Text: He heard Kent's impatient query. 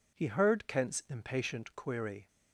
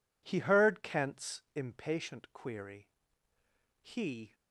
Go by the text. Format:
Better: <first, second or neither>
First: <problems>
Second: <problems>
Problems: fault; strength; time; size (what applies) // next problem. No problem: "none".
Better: first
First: none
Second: goes on to say "He"; from 3.8 s on; 0.52 s long